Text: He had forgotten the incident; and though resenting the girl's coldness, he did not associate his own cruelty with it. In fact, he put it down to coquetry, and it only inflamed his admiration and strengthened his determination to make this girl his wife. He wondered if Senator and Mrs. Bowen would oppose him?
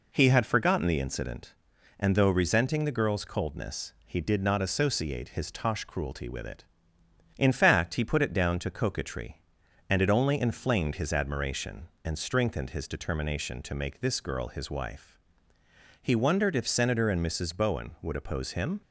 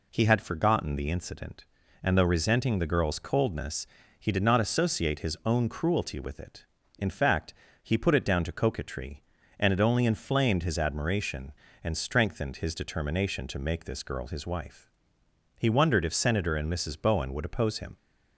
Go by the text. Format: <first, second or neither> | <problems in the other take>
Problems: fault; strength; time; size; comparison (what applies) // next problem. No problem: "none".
second | says "tosh" for "own"; at 5.5 s